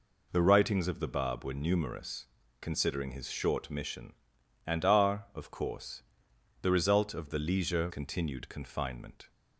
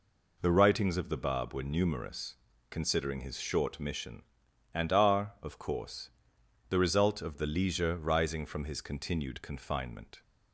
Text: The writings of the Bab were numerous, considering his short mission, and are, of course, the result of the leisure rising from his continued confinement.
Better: second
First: skips "rising from his"; at 7.8 s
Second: none

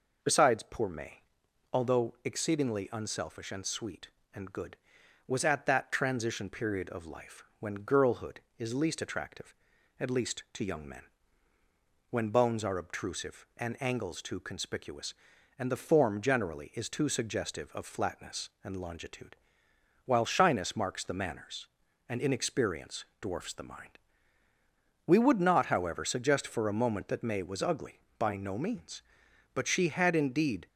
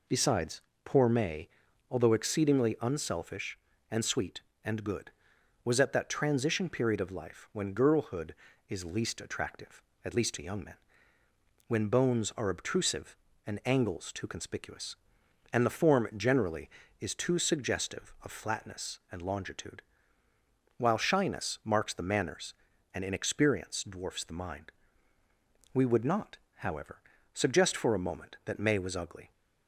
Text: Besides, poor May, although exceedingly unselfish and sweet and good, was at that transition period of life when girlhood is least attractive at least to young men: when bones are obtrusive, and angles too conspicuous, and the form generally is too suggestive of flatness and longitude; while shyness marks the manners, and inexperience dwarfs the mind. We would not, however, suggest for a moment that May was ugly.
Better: second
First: pauses between "life" and "when"; slight; at 7.4 s; 0.16 s long // pauses between "inexperience" and "dwarfs"; slight; at 23.0 s; 0.16 s long // goes on to say "By no means but she had indeed"; strong; from 28.1 s on; 2.4 s long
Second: none

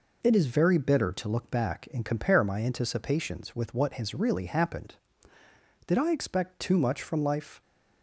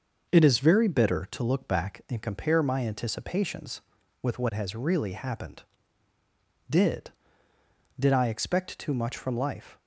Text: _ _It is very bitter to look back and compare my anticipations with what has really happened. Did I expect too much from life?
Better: first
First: none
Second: starts louder than the rest; noticeable; until 1.3 s; 6 dB // says "Did" twice; at 7.9 s

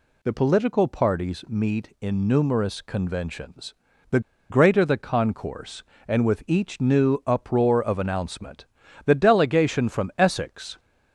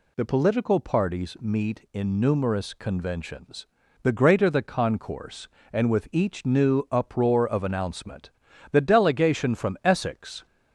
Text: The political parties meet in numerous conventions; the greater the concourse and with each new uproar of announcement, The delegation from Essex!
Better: second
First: pauses between "the" and "greater"; slight; at 4.1 s; 0.30 s long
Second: none

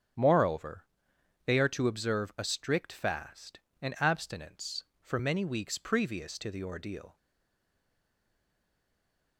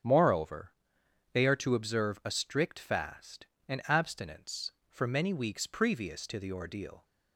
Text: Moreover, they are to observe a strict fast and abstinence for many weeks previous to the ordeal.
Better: second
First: starts louder than the rest; strong; until 1.7 s; 9 dB // stays silent after the last word; from 7.1 s on; 2.2 s long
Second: starts louder than the rest; strong; until 1.6 s; 9 dB

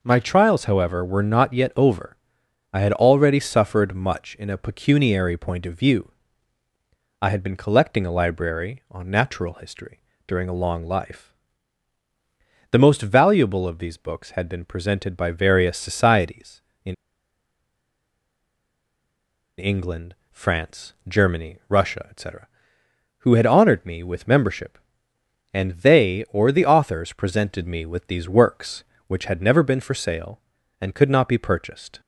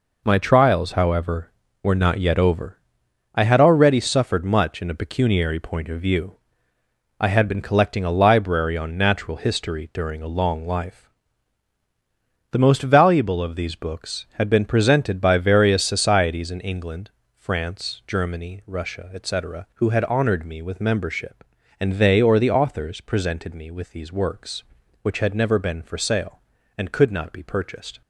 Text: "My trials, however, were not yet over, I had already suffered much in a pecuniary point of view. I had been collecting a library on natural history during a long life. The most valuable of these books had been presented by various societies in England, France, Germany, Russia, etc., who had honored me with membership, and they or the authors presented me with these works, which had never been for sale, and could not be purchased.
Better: second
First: pauses between "history" and "during"; slight; at 9.9 s; 0.26 s long // pauses between "in" and "England"; strong; at 16.9 s; 2.6 s long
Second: none

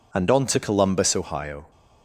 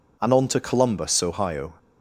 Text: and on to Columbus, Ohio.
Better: neither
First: none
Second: none

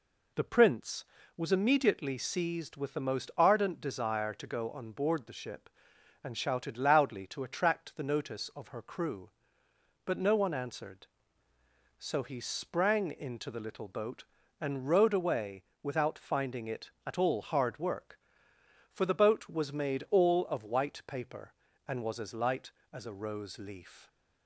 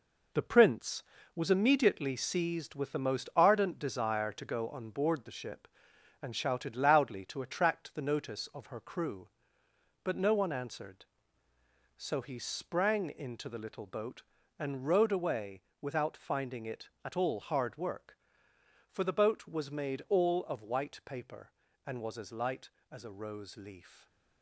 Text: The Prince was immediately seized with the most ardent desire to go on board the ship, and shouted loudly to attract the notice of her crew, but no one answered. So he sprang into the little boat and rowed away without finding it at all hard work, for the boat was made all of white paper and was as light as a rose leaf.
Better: first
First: pauses between "away" and "without"; slight; at 15.6 s; 0.20 s long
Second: gets quieter; throughout; 7 dB // pauses between "away" and "without"; slight; at 15.6 s; 0.20 s long // stays silent after the last word; slight; from 23.8 s on; 0.6 s long

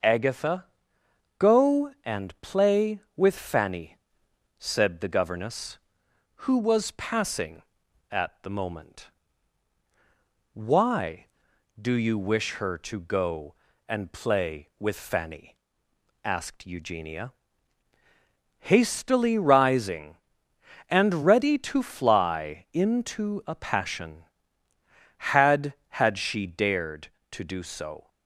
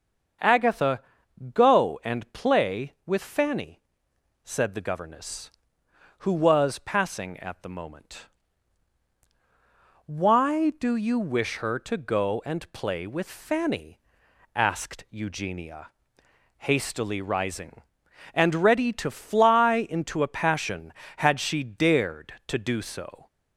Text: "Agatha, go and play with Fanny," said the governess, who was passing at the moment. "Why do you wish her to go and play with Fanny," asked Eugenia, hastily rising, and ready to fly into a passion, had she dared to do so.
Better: second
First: starts louder than the rest; noticeable; until 1.7 s; 6 dB // says "had" twice; at 26.0 s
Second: starts louder than the rest; until 1.9 s; 7 dB

